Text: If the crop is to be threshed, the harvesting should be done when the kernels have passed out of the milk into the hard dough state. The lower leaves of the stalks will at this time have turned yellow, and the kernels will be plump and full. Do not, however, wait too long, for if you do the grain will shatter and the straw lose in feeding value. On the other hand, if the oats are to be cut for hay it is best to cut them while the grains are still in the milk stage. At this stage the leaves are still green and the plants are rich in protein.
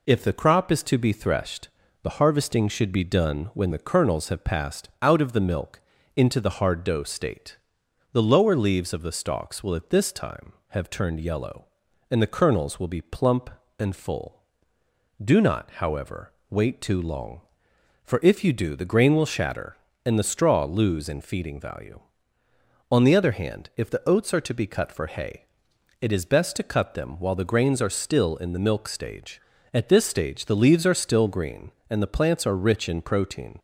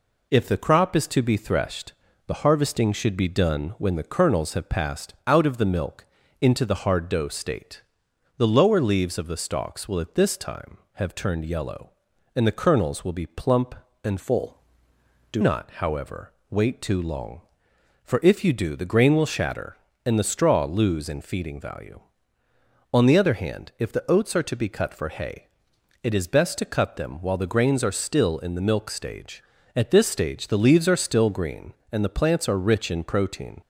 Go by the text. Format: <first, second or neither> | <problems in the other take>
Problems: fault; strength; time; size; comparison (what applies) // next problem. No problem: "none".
first | pauses between "milk" and "into"; slight; at 6.0 s; 0.36 s long; slight in the first // changes voice from "full" to "Do"; from 14.1 to 15.4 s; 1.3 s long // pauses between "hay" and "it"; noticeable; at 25.4 s; 0.56 s long; noticeable in the first